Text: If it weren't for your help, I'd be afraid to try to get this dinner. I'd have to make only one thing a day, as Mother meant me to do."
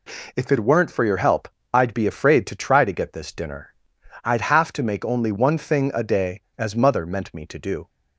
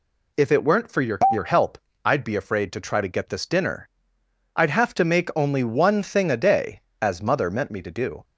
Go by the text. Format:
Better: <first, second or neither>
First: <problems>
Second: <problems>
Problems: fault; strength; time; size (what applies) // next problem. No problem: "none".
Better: first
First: none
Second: says "your" twice; at 1.3 s